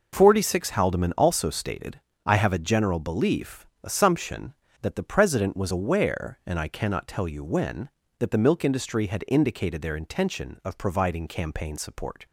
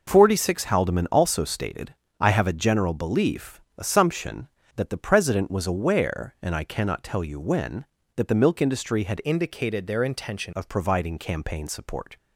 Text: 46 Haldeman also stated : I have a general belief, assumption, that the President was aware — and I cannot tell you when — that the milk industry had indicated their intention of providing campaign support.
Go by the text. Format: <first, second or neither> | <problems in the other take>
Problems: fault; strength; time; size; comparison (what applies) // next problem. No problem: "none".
first | changes voice from "indicated" to "intention"; from 9.2 to 10.5 s; 1.3 s long